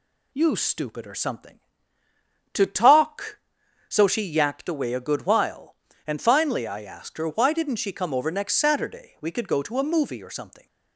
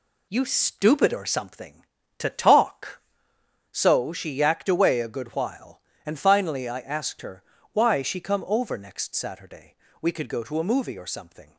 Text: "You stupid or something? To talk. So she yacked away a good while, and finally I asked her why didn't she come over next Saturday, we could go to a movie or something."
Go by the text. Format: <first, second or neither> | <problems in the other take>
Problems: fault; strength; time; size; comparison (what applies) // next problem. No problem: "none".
first | pauses between "her" and "why"; slight; at 7.4 s; 0.30 s long // skips "didn't"; at 8.0 s